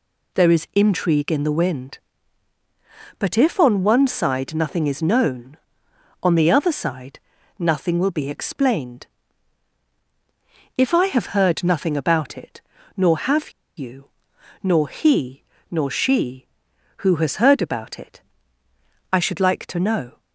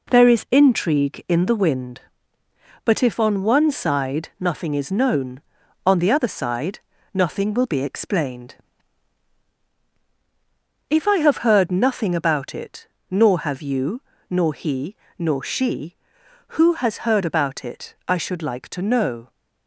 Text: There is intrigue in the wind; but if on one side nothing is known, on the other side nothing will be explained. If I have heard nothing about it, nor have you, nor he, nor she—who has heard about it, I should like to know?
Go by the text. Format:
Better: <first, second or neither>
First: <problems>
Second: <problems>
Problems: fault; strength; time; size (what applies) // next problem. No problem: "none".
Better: second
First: pauses between "side" and "nothing"; at 7.1 s; 0.40 s long // pauses between "have" and "you"; slight; at 13.4 s; 0.27 s long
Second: pauses between "side" and "nothing"; slight; at 6.7 s; 0.34 s long